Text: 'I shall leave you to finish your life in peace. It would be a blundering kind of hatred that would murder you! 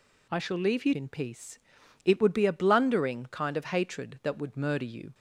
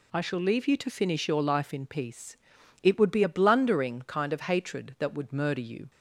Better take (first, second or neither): second